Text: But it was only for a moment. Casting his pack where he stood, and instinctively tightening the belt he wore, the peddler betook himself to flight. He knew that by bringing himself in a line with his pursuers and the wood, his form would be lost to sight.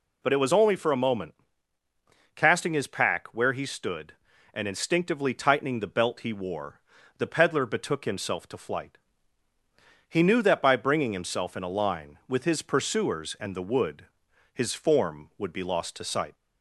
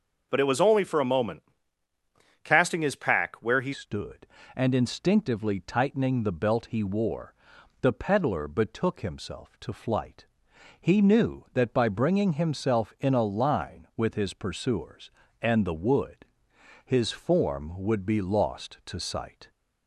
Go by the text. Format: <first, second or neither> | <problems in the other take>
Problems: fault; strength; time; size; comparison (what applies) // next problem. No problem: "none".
first | starts louder than the rest; until 1.3 s; 6 dB // changes voice at "stood"; from 3.7 s on; 15.7 s long